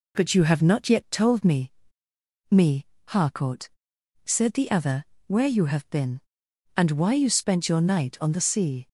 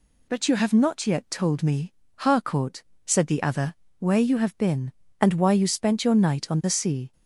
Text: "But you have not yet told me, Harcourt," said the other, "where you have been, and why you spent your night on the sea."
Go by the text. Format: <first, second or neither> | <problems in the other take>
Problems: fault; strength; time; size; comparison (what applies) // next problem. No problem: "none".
second | says "me" twice; at 2.4 s